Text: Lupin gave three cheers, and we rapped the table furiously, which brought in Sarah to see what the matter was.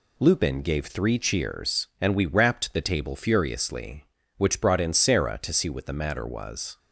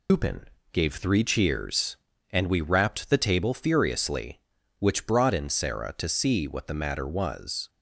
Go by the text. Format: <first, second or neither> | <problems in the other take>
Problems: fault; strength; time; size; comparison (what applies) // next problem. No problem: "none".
first | loses the start of "Lupin"; at 0.0 s; 130 ms // pauses between "Lupin" and "gave"; slight; at 0.4 s; 0.28 s long